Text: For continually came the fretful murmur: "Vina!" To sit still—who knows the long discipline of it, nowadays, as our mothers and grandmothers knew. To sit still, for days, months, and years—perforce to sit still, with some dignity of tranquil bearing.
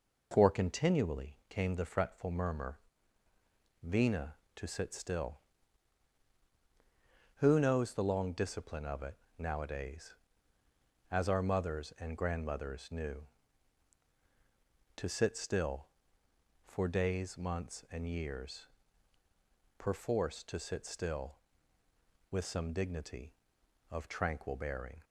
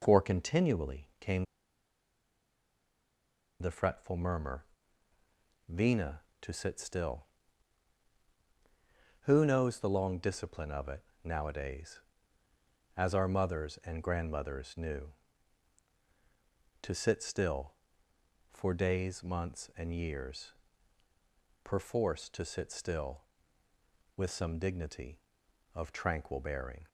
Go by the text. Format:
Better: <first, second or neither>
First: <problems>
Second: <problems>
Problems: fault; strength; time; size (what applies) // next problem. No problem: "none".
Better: first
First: none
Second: pauses between "came" and "the"; strong; at 1.4 s; 2.1 s long